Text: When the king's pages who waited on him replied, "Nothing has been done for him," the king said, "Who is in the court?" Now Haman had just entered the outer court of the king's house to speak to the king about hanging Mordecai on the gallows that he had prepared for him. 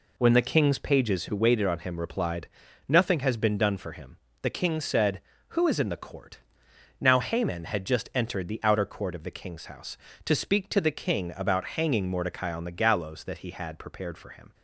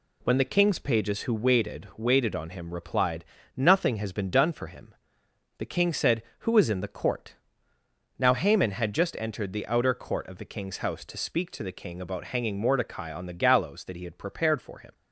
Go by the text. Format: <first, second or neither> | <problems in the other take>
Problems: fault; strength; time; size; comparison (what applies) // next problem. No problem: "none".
first | says "waited" twice; at 1.9 s